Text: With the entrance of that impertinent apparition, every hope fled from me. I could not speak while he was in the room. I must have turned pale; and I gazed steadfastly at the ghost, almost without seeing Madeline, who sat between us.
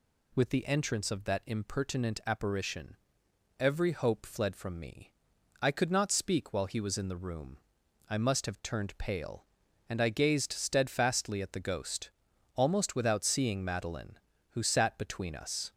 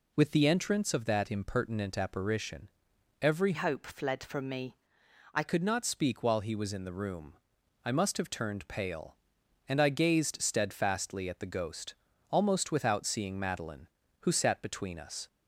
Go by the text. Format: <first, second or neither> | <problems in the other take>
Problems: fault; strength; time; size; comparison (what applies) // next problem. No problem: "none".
first | changes voice from "hope" to "I"; from 3.5 to 5.4 s; 1.9 s long